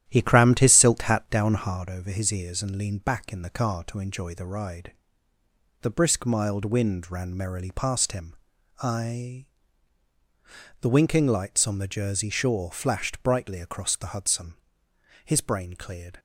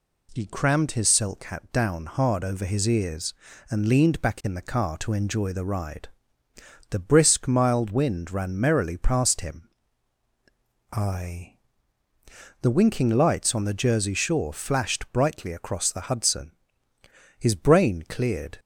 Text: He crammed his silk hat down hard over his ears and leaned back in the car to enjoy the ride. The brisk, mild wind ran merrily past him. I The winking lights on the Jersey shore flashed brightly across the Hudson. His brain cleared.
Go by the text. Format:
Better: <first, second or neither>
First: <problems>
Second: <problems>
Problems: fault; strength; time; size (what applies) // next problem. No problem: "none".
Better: second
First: starts louder than the rest; strong; until 1.8 s; 11.5 dB // pauses between "I" and "The"; strong; at 9.4 s; 1.3 s long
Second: pauses between "I" and "The"; at 11.5 s; 1.0 s long